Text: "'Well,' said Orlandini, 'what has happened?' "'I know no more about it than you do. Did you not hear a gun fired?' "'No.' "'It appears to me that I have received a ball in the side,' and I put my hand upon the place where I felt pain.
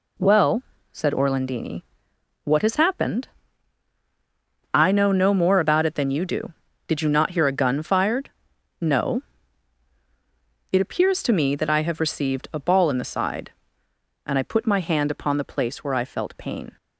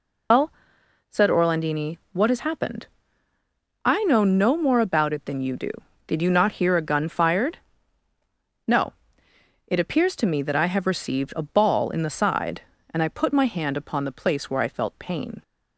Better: first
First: none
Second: loses the start of "Well"; at 0.3 s; 145 ms

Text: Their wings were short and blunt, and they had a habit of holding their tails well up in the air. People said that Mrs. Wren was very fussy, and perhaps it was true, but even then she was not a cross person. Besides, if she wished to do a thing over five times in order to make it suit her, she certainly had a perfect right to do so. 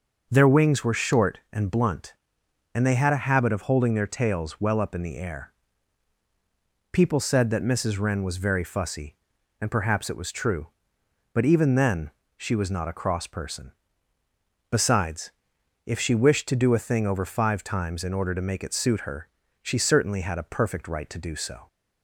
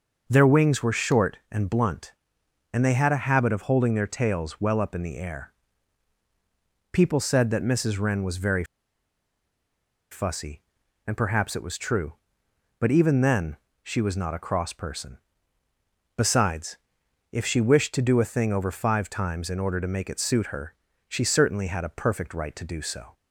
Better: first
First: pauses between "then" and "she"; slight; at 12.0 s; 0.28 s long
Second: pauses between "very" and "fussy"; strong; at 8.6 s; 1.4 s long // pauses between "then" and "she"; slight; at 13.5 s; 0.28 s long

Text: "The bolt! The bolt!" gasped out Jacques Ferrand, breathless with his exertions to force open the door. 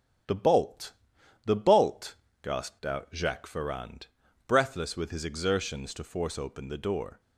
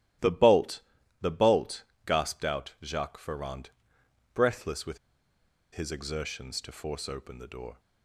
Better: first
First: starts louder than the rest; until 1.7 s; 7 dB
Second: starts louder than the rest; strong; until 1.6 s; 14.5 dB // pauses between "with" and "his"; noticeable; at 4.9 s; 0.75 s long

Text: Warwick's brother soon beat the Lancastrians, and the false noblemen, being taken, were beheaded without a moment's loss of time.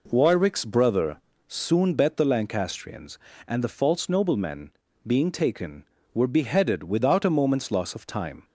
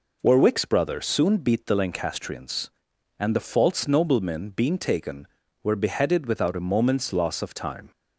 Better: second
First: pauses between "brother" and "soon"; slight; at 1.1 s; 0.30 s long // says "bet" for "beat"; at 1.9 s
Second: none

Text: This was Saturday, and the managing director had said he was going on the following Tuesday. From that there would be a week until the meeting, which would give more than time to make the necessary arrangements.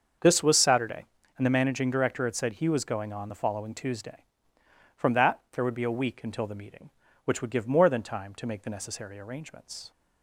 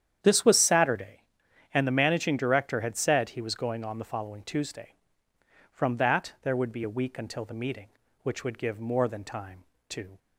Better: first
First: starts louder than the rest; until 1.5 s; 6.5 dB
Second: starts louder than the rest; strong; until 1.2 s; 9.5 dB // stops before "make the necessary arrangements"; at 10.1 s

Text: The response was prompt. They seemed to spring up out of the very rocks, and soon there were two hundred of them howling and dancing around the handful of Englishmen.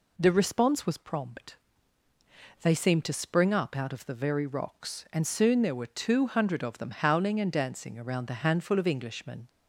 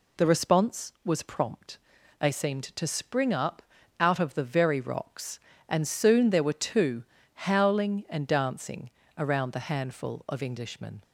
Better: first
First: none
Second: pauses between "up" and "out"; slight; at 3.6 s; 0.36 s long // skips "hundred of them"; at 7.1 s // pauses between "dancing" and "around"; slight; at 8.8 s; 0.28 s long

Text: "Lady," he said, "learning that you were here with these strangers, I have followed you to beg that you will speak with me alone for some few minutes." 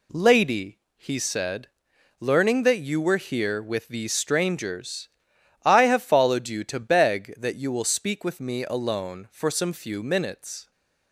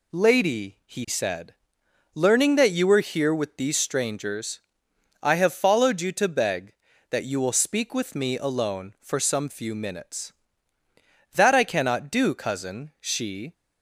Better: first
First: none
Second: goes on to say "That I cannot do cousin she"; strong; from 11.3 s on; 2.1 s long

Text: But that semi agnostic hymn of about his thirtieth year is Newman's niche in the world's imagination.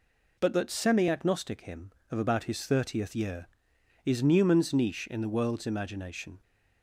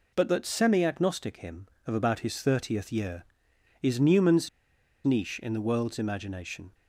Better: first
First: none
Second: pauses between "Newman's" and "niche"; noticeable; at 4.4 s; 0.56 s long

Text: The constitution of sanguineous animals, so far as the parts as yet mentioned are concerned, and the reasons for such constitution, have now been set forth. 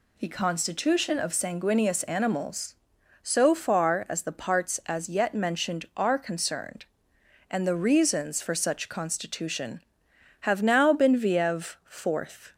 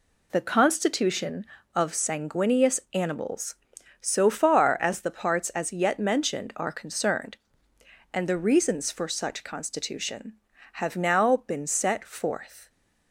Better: second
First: says "viev" for "set"; at 11.1 s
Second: none

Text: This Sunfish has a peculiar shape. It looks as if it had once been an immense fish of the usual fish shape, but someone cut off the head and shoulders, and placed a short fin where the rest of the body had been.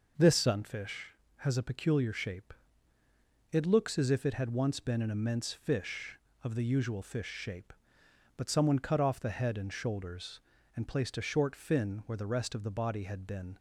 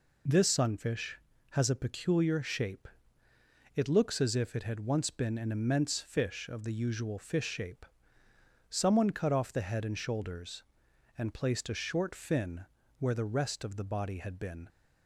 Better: first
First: none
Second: skips "but"; at 8.2 s // pauses between "fin" and "where"; slight; at 12.6 s; 0.36 s long

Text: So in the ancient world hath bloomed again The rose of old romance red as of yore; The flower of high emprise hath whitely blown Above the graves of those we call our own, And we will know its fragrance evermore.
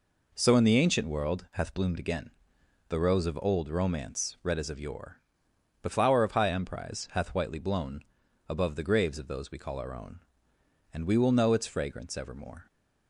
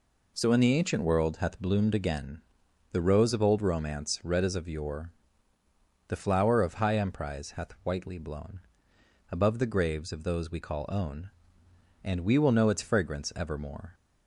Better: first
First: pauses between "again" and "The"; noticeable; at 2.3 s; 0.58 s long // pauses between "blown" and "Above"; at 8.0 s; 0.44 s long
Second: pauses between "again" and "The"; noticeable; at 2.4 s; 0.48 s long // pauses between "blown" and "Above"; noticeable; at 8.5 s; 0.72 s long // skips "our"; at 10.8 s

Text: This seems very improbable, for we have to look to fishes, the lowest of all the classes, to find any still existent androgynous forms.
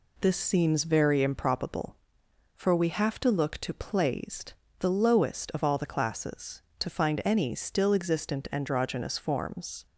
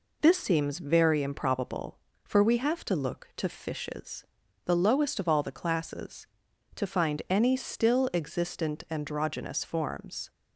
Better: second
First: says "plaised" for "fishes"; at 3.7 s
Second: none

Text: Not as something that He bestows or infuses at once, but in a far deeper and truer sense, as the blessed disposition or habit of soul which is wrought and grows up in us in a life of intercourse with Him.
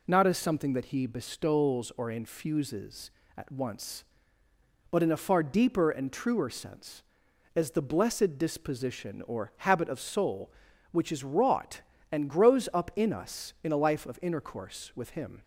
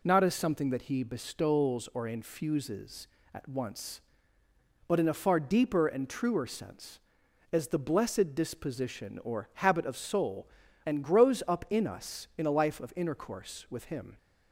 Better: first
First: none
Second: skips "which is wrought"; at 10.6 s

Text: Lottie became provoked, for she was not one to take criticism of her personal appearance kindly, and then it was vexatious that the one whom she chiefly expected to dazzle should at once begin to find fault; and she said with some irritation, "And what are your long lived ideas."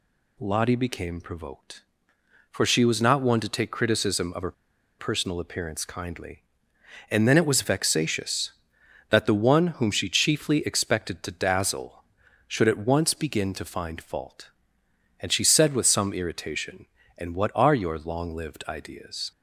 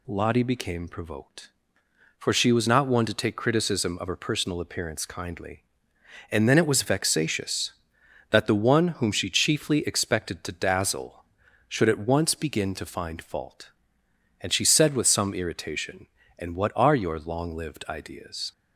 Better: second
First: pauses between "her" and "personal"; noticeable; at 4.5 s; 0.46 s long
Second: none

